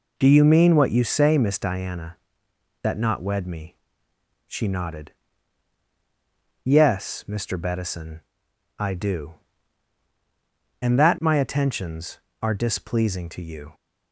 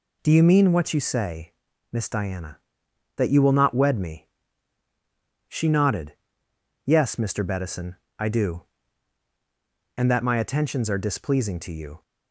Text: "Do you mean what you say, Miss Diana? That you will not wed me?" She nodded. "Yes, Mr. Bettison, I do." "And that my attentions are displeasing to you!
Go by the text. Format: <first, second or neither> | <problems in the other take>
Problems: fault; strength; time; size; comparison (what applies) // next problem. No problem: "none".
second | skips "you will"; at 2.9 s